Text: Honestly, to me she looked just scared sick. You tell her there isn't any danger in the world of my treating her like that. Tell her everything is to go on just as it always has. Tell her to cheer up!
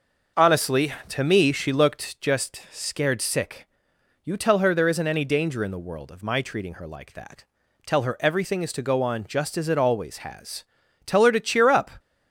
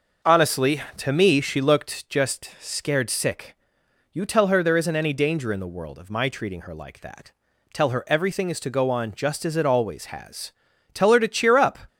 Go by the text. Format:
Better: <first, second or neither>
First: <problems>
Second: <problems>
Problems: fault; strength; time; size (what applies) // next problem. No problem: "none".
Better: neither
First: starts louder than the rest; until 1.5 s; 6 dB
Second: starts louder than the rest; until 1.4 s; 6 dB